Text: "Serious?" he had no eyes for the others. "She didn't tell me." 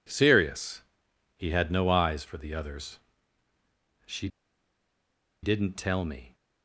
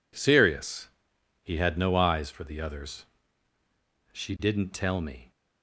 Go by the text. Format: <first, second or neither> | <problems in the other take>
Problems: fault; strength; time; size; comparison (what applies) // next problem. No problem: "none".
second | pauses between "She" and "didn't"; at 4.2 s; 1.1 s long